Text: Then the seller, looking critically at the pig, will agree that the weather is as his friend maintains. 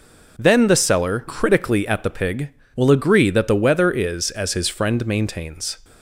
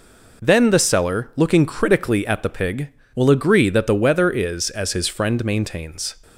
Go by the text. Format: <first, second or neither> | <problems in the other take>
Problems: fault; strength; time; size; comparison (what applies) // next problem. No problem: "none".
second | skips "looking"; at 1.2 s